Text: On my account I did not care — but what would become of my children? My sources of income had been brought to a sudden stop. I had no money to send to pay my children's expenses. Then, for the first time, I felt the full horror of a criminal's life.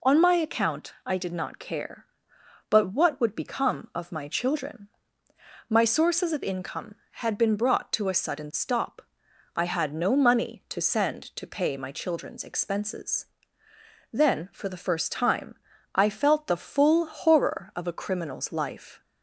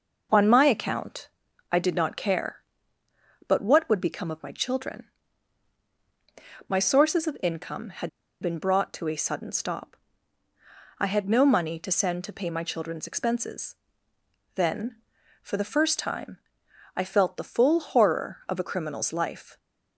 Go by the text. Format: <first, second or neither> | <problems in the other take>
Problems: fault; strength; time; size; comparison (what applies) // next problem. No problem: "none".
first | pauses between "account" and "I"; at 1.2 s; 0.44 s long // pauses between "had" and "been"; slight; at 8.0 s; 0.33 s long